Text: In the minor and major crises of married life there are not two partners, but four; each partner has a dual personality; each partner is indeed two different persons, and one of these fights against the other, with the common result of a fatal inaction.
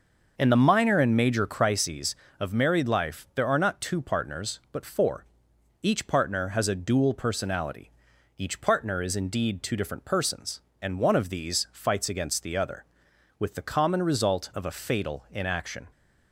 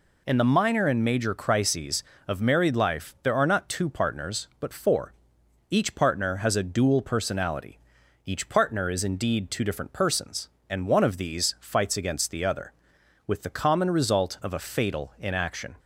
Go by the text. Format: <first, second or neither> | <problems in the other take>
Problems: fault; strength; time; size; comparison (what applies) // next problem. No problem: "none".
second | starts louder than the rest; noticeable; until 1.7 s; 6 dB